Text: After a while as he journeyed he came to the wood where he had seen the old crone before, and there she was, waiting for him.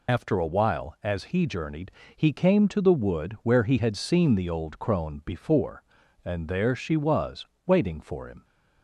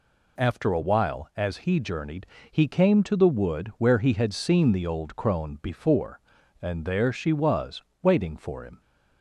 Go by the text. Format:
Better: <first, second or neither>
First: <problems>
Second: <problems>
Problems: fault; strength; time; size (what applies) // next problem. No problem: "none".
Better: second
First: loses the start of "After"; at 0.0 s; 50 ms // pauses between "journeyed" and "he"; slight; at 1.8 s; 0.26 s long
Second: pauses between "journeyed" and "he"; slight; at 2.2 s; 0.26 s long